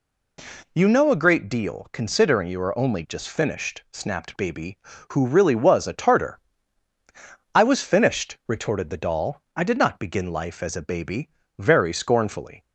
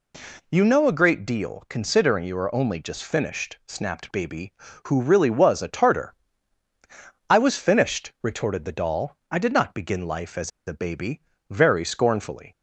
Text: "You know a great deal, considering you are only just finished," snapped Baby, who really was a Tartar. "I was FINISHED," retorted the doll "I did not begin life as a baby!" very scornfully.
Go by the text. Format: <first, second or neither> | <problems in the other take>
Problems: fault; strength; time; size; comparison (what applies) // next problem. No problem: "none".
first | pauses between "as" and "a"; slight; at 10.4 s; 0.17 s long